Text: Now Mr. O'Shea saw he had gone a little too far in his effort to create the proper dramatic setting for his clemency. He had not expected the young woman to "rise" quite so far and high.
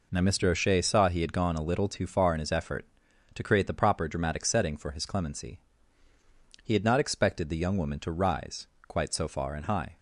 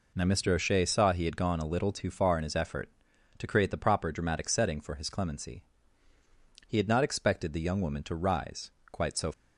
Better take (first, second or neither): first